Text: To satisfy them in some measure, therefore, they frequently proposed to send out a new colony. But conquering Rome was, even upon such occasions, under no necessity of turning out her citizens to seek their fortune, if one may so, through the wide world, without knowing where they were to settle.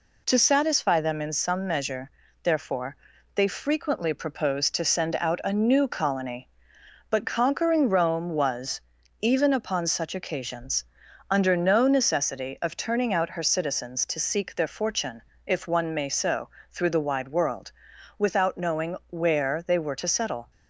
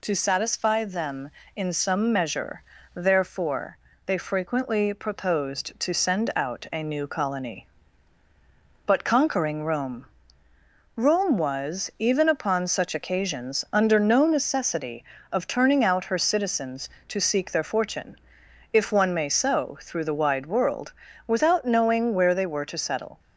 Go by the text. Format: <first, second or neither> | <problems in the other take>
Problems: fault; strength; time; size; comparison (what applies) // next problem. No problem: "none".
first | says "Rome" twice; at 10.9 s